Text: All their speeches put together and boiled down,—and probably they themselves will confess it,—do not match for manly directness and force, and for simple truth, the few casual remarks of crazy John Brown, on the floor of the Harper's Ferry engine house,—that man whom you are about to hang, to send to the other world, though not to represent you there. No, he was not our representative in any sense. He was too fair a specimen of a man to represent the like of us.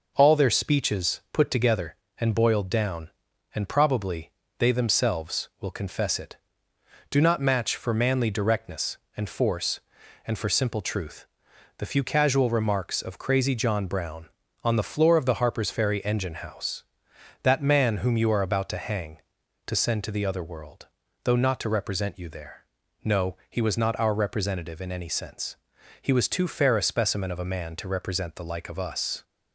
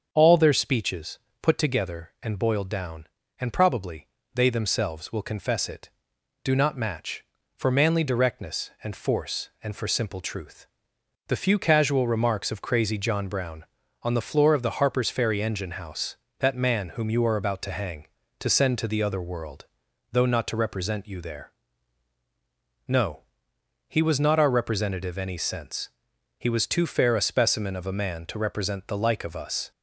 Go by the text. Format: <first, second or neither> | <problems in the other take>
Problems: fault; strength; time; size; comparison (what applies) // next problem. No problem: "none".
first | starts louder than the rest; until 1.1 s; 7 dB // pauses between "speeches" and "put"; slight; at 1.1 s; 0.22 s long // pauses between "probably" and "they"; slight; at 4.0 s; 0.26 s long; slight in the first // skips "in"; at 25.1 s